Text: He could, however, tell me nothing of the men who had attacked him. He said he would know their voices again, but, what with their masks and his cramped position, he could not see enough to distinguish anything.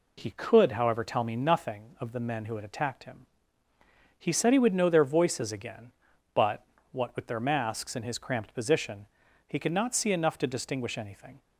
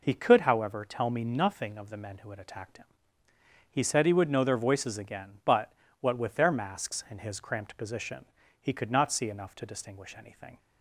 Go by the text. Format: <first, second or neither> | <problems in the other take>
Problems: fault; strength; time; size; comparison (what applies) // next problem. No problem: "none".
neither | none